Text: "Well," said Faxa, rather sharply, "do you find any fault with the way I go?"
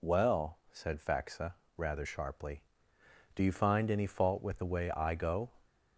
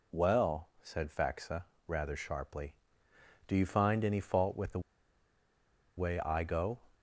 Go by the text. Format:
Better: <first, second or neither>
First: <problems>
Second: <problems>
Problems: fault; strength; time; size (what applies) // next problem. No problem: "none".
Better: first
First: none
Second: pauses between "the" and "way"; at 4.8 s; 1.1 s long